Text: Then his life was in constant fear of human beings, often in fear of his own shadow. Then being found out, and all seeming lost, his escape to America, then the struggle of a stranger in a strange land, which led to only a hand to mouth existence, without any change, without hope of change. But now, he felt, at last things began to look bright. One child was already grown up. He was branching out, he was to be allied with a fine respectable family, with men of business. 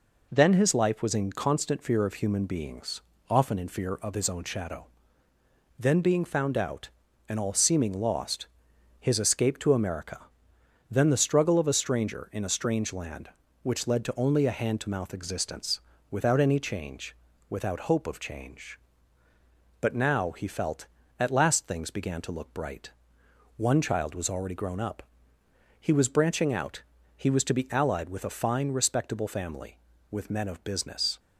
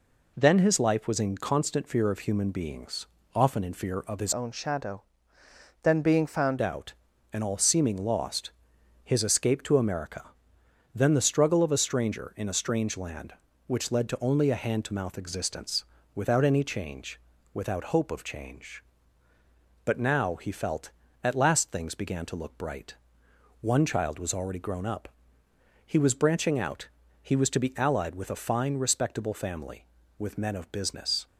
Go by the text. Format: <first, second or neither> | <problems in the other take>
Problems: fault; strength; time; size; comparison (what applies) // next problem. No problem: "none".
first | changes voice from "own" to "found"; from 4.3 to 6.6 s; 2.3 s long